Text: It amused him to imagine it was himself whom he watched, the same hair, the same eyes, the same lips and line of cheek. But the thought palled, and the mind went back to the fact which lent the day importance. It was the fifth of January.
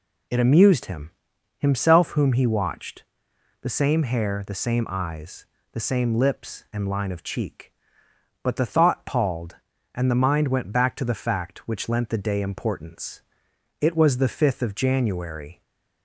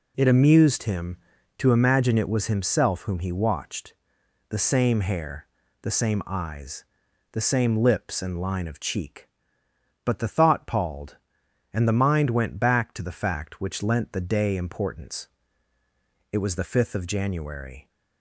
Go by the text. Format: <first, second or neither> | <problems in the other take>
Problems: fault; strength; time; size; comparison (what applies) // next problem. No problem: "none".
second | skips "to imagine it was"; at 1.3 s // stays silent after the last word; slight; from 15.5 s on; 0.5 s long